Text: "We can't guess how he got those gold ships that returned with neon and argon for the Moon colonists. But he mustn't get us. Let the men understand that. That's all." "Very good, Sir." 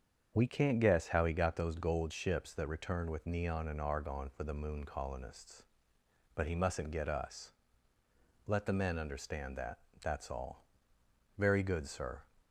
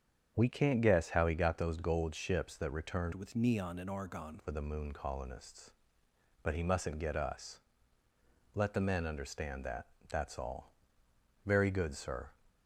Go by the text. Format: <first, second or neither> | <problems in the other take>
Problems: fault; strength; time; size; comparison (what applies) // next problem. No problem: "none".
first | starts louder than the rest; strong; until 1.3 s; 7.5 dB; strong in the first // changes voice from "with" to "argon"; from 3.1 to 4.3 s; 1.2 s long